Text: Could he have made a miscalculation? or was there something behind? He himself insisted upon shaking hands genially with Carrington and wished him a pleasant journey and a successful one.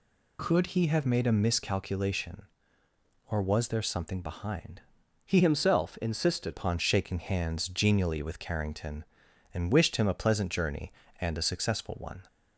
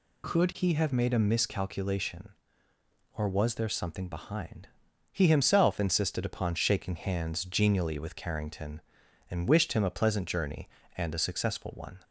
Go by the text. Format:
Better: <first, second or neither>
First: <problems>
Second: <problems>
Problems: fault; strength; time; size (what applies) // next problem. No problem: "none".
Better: second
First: changes voice from "himself" to "insisted"; from 5.3 to 6.5 s; 1.2 s long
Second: none